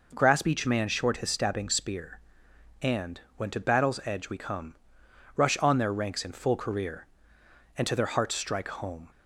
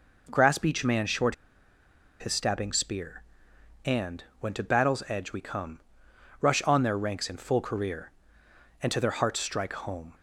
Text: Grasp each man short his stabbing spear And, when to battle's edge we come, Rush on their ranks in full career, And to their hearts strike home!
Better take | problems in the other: first | pauses between "short" and "his"; noticeable; at 1.3 s; 0.85 s long

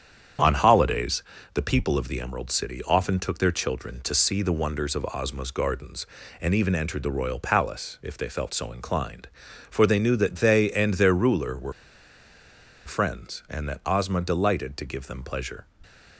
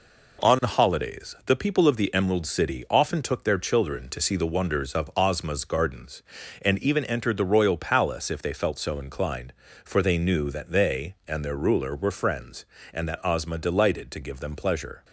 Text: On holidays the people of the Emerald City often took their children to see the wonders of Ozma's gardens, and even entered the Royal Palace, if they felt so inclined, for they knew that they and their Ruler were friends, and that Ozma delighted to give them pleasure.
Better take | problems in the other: second | starts louder than the rest; strong; until 1.7 s; 8.5 dB // pauses between "holidays" and "the"; slight; at 1.2 s; 0.30 s long // pauses between "were" and "friends"; at 11.7 s; 1.1 s long

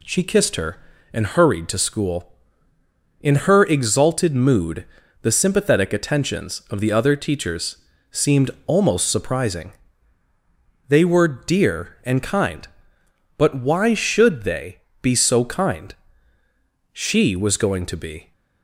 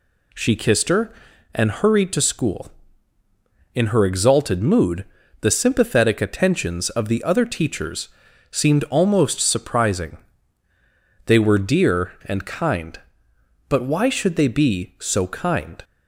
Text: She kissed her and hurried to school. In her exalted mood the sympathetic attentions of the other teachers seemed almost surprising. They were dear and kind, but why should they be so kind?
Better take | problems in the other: second | pauses between "mood" and "the"; slight; at 4.8 s; 0.36 s long; also in the second // pauses between "teachers" and "seemed"; slight; at 7.7 s; 0.34 s long; also in the second // pauses between "seemed" and "almost"; slight; at 8.4 s; 0.16 s long // pauses between "they" and "be"; slight; at 14.7 s; 0.24 s long // goes on to say "She was going to be"; from 16.9 s on; 1.4 s long

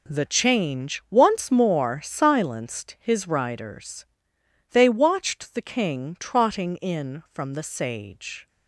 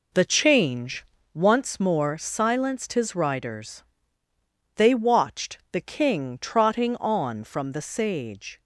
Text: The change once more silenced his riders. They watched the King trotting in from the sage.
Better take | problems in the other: first | pauses between "change" and "once"; slight; at 1.0 s; 0.26 s long // pauses between "watched" and "the"; slight; at 5.5 s; 0.16 s long // says "on" for "in"; at 6.9 s

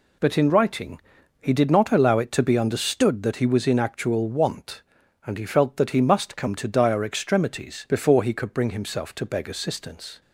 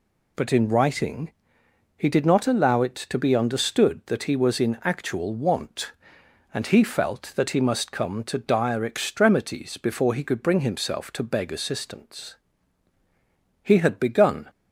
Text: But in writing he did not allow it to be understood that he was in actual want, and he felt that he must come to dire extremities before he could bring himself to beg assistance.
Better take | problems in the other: first | pauses between "writing" and "he"; noticeable; at 1.3 s; 0.66 s long; also in the first // goes on to say "He had begun"; noticeable; from 13.6 s on; 0.86 s long

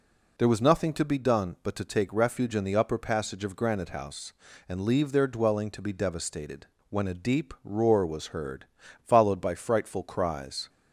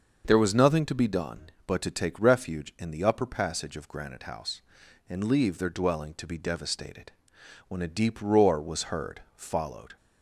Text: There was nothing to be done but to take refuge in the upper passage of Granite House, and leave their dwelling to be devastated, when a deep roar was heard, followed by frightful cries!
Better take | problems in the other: first | starts louder than the rest; until 1.2 s; 6 dB // stops before "by frightful cries"; at 9.9 s

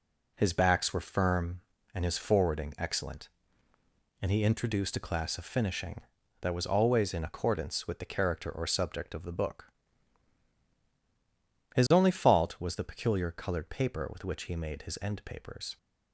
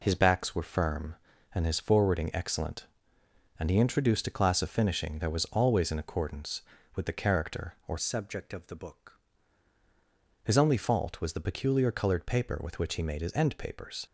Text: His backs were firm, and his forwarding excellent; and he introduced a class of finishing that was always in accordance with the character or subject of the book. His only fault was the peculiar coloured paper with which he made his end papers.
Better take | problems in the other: first | changes voice from "subject" to "book"; from 7.9 to 9.2 s; 1.3 s long

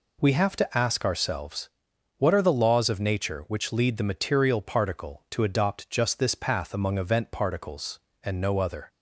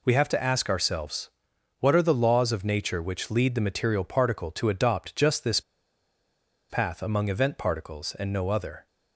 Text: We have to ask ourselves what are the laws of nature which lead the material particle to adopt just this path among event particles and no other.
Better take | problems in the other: first | pauses between "ourselves" and "what"; noticeable; at 1.2 s; 0.50 s long; noticeable in the first // pauses between "this" and "path"; at 5.6 s; 1.0 s long

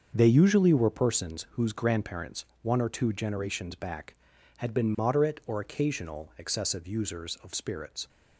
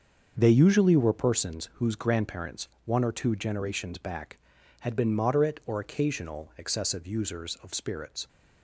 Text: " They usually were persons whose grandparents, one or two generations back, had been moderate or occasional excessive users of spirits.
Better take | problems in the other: neither | starts louder than the rest; the same in both

